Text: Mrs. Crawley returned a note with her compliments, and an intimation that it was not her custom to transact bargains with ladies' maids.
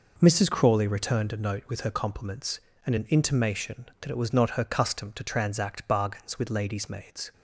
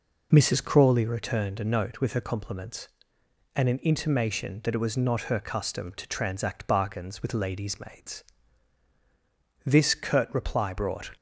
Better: first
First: none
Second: goes on to say "This curt reply brought"; from 9.6 s on; 1.4 s long

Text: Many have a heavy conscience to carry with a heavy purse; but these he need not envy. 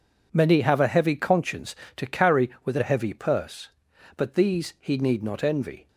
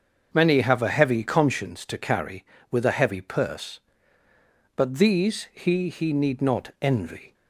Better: first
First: none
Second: starts louder than the rest; until 1.3 s; 6.5 dB // says "he" twice; at 5.8 s

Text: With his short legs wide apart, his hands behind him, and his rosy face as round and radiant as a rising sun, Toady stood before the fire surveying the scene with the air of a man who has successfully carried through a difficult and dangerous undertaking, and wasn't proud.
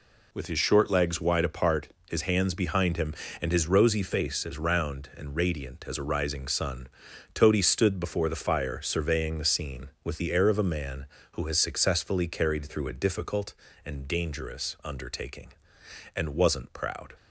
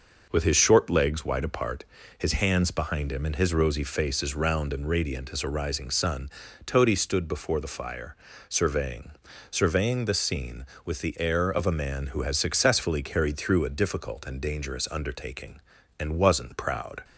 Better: first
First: none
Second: pauses between "fire" and "surveying"; slight; at 8.1 s; 0.36 s long // says "surveying" twice; at 9.4 s

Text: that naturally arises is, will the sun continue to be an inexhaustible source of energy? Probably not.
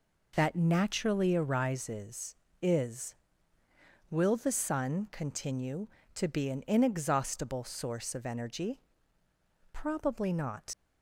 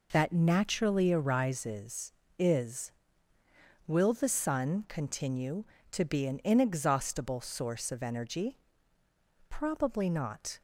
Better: second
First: leaves "not" unfinished; at 10.7 s; 110 ms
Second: none

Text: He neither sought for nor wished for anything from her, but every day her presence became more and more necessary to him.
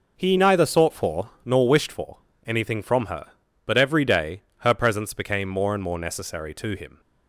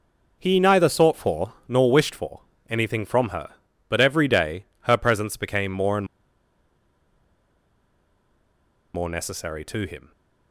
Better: first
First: pauses between "for" and "nor"; slight; at 1.2 s; 0.16 s long // pauses between "for" and "anything"; slight; at 2.1 s; 0.30 s long // pauses between "day" and "her"; slight; at 4.4 s; 0.18 s long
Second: pauses between "for" and "nor"; slight; at 1.5 s; 0.16 s long // pauses between "for" and "anything"; slight; at 2.3 s; 0.30 s long // pauses between "day" and "her"; slight; at 4.6 s; 0.18 s long // pauses between "and" and "more"; strong; at 6.0 s; 2.8 s long

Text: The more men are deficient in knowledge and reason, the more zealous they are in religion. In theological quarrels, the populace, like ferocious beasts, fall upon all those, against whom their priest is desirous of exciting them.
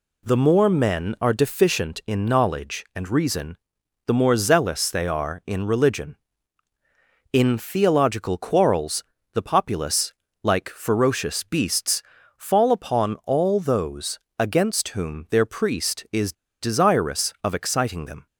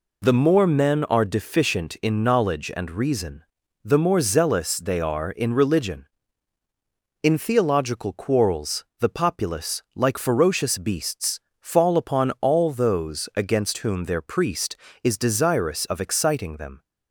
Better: second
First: pauses between "is" and "desirous"; slight; at 16.3 s; 0.29 s long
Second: none

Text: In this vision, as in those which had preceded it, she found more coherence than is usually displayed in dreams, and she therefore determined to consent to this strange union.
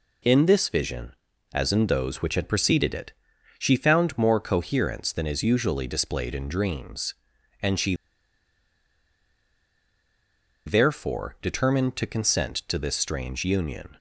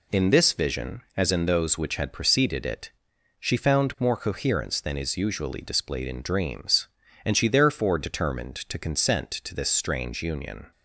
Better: second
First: pauses between "she" and "therefore"; strong; at 7.9 s; 2.7 s long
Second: none

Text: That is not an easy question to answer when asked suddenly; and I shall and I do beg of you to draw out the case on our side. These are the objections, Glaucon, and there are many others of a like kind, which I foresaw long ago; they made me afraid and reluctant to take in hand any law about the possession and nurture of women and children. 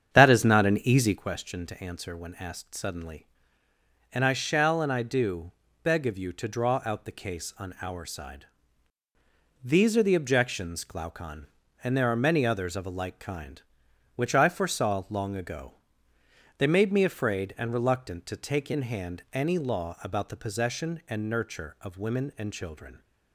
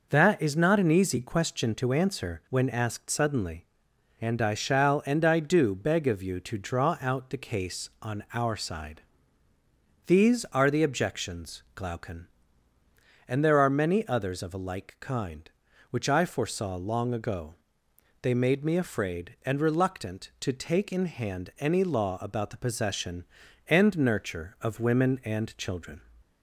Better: second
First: starts louder than the rest; strong; until 1.3 s; 8 dB // pauses between "do" and "beg"; slight; at 5.5 s; 0.32 s long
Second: none

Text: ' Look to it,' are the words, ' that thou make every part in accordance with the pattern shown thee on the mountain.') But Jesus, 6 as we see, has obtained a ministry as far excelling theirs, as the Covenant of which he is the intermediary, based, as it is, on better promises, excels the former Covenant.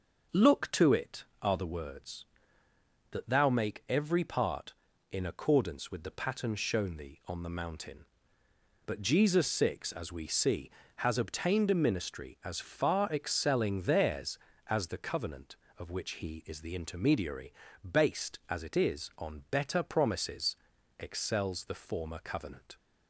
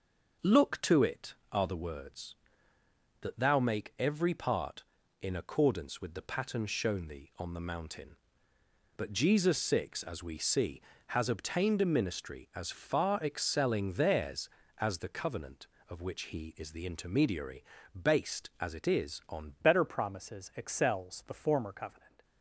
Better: first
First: none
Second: changes voice at "better"; from 19.6 s on; 2.6 s long

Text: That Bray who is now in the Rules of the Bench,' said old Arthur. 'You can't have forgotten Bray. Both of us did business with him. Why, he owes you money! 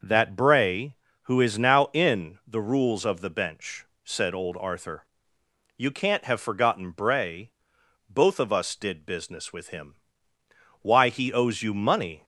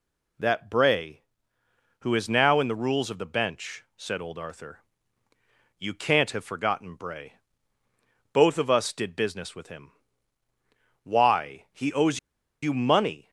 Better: first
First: none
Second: pauses between "owes" and "you"; at 12.1 s; 0.44 s long

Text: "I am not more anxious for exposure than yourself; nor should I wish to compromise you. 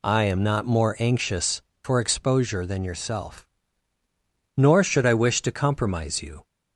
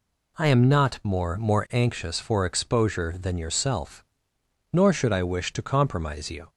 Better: first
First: none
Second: says "more" twice; at 1.3 s

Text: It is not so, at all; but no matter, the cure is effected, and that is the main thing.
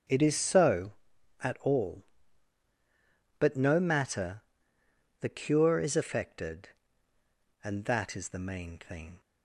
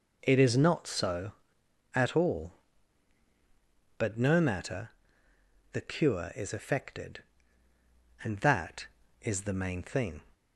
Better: second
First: starts louder than the rest; strong; until 1.5 s; 8.5 dB // skips "not"; at 0.3 s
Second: none

